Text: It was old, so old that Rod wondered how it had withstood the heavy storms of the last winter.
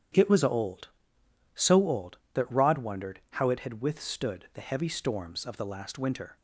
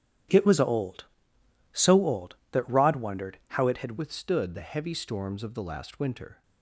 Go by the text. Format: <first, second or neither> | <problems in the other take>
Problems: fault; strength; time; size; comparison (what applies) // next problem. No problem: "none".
first | starts louder than the rest; strong; until 1.9 s; 10.5 dB; strong in the first // changes voice at "withstood"; from 3.9 s on; 2.5 s long